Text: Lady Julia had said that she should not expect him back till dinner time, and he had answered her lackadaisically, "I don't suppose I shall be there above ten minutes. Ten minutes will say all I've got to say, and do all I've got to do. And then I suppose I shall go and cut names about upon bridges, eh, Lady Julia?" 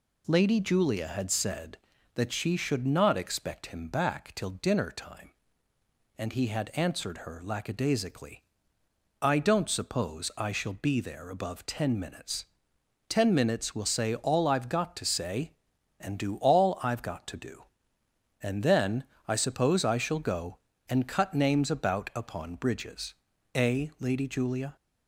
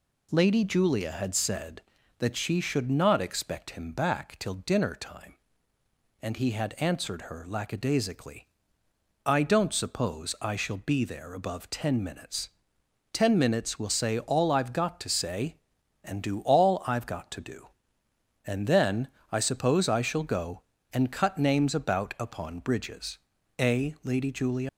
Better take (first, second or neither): first